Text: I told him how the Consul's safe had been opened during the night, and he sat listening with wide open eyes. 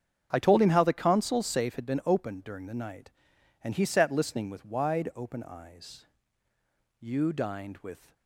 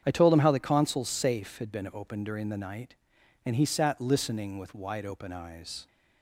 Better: second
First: starts louder than the rest; strong; until 1.3 s; 8 dB // goes on to say "You dined with"; noticeable; from 7.0 s on; 1.1 s long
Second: starts louder than the rest; strong; until 1.0 s; 8 dB

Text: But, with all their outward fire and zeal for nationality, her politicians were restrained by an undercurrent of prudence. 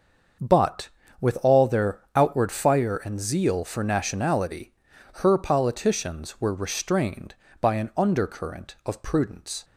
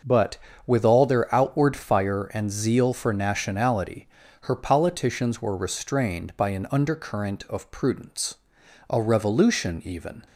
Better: first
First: starts louder than the rest; until 1.7 s; 6.5 dB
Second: starts louder than the rest; until 1.3 s; 6.5 dB // goes on to say "A revolution even"; from 8.8 s on; 1.3 s long

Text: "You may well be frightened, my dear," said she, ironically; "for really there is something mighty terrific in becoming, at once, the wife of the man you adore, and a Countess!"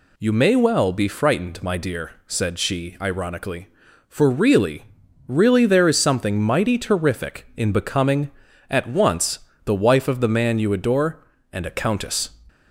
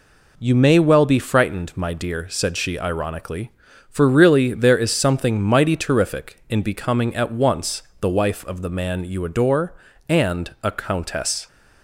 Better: second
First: says "really" twice; at 5.2 s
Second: none

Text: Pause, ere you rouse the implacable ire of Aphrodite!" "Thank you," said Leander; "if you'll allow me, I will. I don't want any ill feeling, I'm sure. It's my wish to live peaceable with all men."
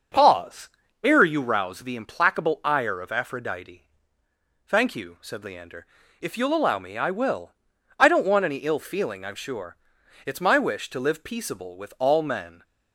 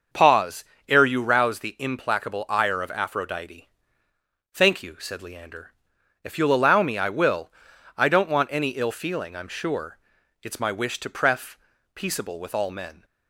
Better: first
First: starts louder than the rest; noticeable; until 1.4 s; 6 dB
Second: starts louder than the rest; until 1.3 s; 6.5 dB // says "pref" for "live"; at 11.0 s

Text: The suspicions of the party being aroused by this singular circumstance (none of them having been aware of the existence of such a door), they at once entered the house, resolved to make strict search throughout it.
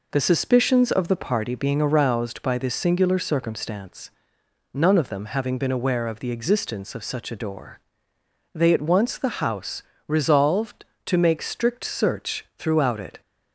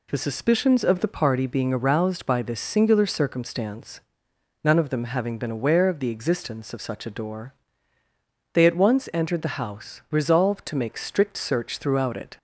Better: second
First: skips "entered"; at 9.1 s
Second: none

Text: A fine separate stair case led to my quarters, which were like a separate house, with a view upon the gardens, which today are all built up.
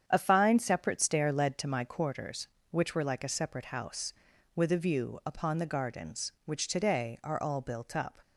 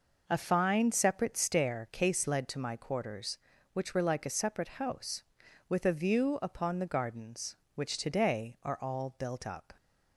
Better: second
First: starts louder than the rest; strong; until 1.0 s; 8.5 dB // skips "case"; at 1.3 s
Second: none

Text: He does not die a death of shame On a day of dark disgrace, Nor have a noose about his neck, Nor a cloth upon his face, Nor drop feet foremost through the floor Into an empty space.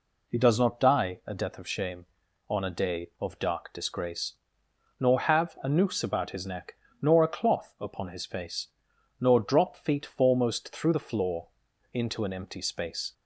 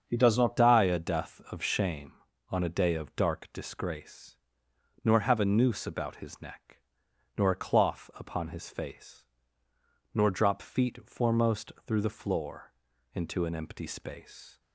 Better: first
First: pauses between "floor" and "Into"; at 11.4 s; 0.44 s long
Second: starts louder than the rest; until 1.0 s; 7 dB // changes voice at "die"; from 0.5 s on; 14.1 s long // pauses between "floor" and "Into"; at 12.7 s; 0.40 s long

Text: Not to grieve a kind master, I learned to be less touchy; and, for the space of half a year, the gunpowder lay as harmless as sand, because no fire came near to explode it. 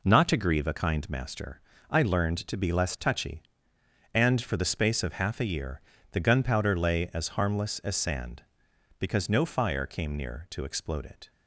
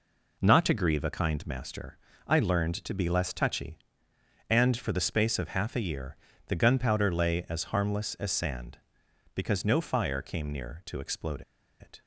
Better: first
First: none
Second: pauses between "explode" and "it"; at 11.4 s; 0.38 s long

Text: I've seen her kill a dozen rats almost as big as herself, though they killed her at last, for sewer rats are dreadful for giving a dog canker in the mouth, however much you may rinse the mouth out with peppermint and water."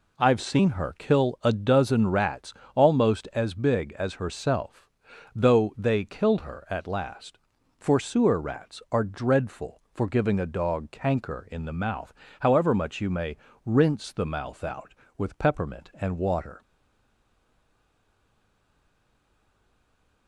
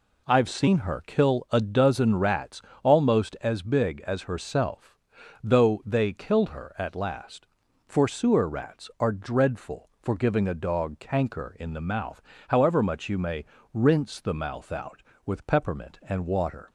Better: second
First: pauses between "rats" and "almost"; slight; at 2.5 s; 0.20 s long // pauses between "may" and "rinse"; slight; at 13.3 s; 0.30 s long // stays silent after the last word; strong; from 16.6 s on; 3.6 s long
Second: pauses between "rats" and "almost"; slight; at 2.6 s; 0.20 s long // pauses between "may" and "rinse"; slight; at 13.4 s; 0.30 s long

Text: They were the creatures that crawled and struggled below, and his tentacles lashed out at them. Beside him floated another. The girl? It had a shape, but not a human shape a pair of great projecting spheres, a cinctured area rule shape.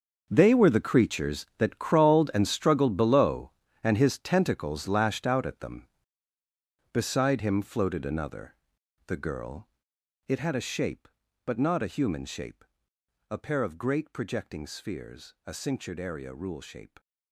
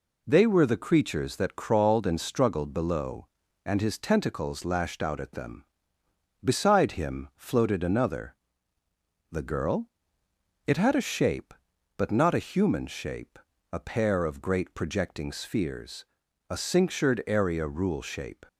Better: second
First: gets quieter; strong; throughout; 15 dB // pauses between "shape" and "a"; noticeable; at 12.6 s; 0.66 s long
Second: pauses between "shape" and "a"; slight; at 13.3 s; 0.34 s long

